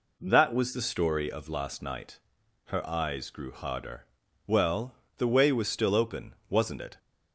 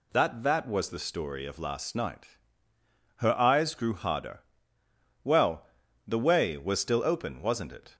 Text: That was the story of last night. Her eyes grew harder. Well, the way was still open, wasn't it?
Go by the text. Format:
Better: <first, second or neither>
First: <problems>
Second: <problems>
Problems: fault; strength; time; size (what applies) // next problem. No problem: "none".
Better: first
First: none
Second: says "That" twice; at 0.4 s